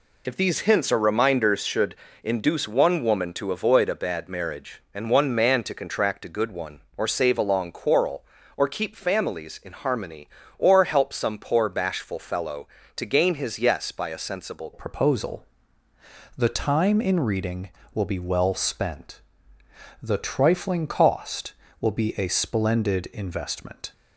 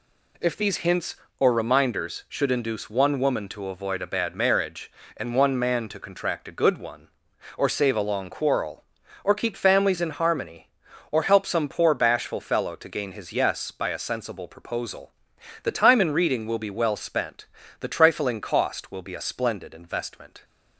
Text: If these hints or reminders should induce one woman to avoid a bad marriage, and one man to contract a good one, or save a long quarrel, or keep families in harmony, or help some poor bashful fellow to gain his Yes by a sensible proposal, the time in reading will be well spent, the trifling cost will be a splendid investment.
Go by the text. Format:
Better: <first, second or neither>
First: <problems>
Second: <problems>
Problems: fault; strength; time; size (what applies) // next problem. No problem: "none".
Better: second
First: pauses between "should" and "induce"; slight; at 1.9 s; 0.30 s long // changes voice at "proposal"; from 14.7 s on; 9.2 s long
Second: none